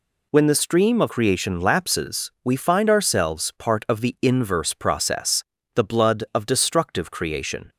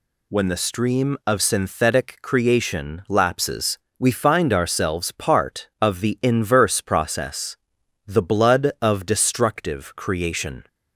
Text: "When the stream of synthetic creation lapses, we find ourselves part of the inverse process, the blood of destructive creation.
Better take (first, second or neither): second